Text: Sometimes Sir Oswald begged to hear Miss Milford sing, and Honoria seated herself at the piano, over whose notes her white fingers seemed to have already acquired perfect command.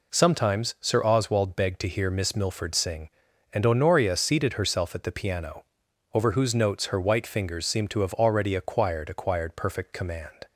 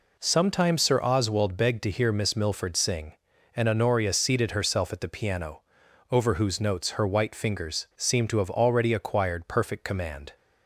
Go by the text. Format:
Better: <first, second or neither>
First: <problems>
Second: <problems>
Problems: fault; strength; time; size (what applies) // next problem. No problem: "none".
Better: second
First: says "acquired" twice; at 9.0 s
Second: none